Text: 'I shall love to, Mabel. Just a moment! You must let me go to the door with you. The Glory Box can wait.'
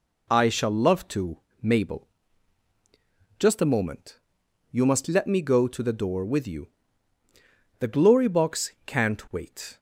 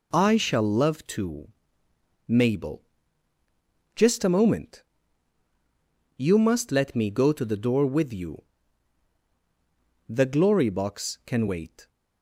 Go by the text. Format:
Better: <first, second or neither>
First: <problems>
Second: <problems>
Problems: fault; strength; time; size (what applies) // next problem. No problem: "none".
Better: second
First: says "can't" for "can"; at 8.8 s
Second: none